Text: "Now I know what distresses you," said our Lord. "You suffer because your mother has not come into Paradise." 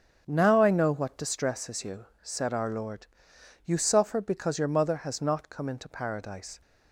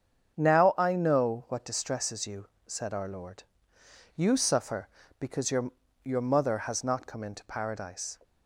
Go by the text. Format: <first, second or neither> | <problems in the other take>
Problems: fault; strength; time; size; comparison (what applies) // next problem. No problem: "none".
first | starts louder than the rest; strong; until 1.4 s; 7.5 dB; strong in the first // says "your" twice; at 6.0 s